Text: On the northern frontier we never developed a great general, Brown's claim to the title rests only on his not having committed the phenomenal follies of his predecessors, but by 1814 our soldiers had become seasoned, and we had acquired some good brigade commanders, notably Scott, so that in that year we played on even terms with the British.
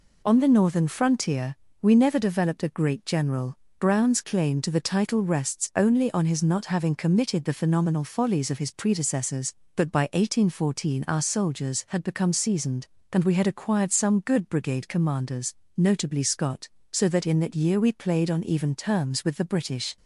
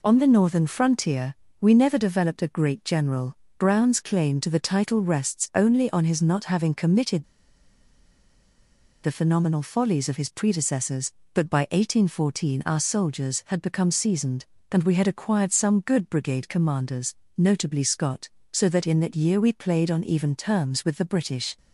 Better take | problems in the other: first | pauses between "frontier" and "we"; slight; at 1.3 s; 0.26 s long; slight in the first // pauses between "committed" and "the"; strong; at 7.2 s; 1.8 s long

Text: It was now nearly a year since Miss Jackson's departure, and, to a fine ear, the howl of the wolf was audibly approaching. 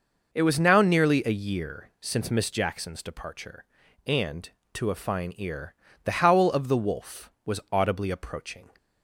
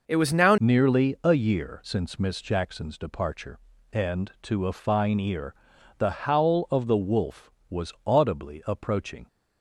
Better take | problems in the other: first | changes voice at "nearly"; from 0.5 s on; 8.7 s long

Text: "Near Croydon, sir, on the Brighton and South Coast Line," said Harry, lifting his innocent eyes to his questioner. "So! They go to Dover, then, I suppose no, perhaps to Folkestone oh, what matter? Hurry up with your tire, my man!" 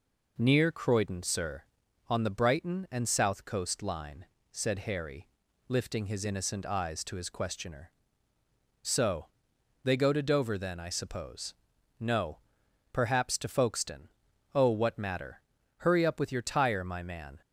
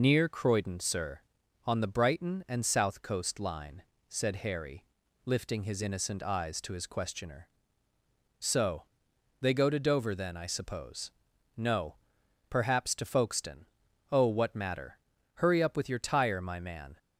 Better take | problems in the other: first | loses the start of "Near"; at 0.0 s; 55 ms // pauses between "suppose" and "no"; at 11.1 s; 0.44 s long; also in the first // pauses between "Folkestone" and "oh"; at 13.6 s; 0.44 s long; also in the first

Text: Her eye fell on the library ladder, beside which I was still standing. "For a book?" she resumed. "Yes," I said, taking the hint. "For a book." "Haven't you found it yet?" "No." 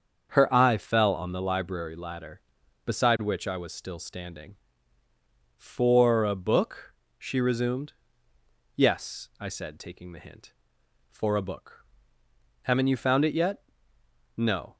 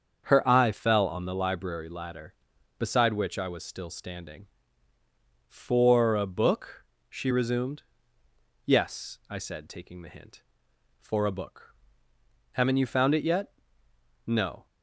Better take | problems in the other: neither | starts louder than the rest; the same in both

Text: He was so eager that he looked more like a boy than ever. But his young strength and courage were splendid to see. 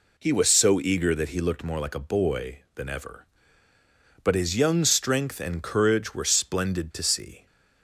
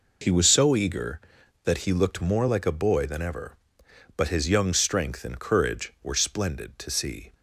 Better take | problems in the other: neither | none

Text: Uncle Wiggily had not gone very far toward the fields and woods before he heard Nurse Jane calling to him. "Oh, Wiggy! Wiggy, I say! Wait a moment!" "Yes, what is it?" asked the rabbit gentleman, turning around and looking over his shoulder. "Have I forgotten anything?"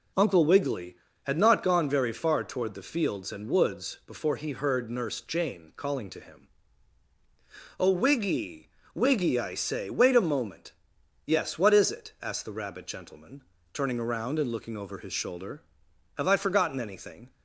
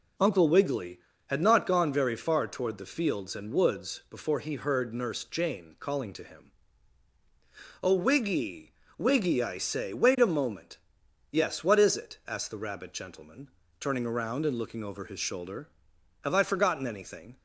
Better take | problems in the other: neither | none

